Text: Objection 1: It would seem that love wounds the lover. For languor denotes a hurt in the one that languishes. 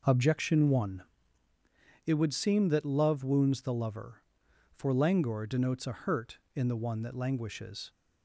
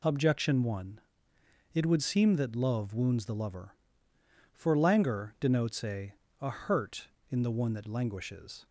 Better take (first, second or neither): first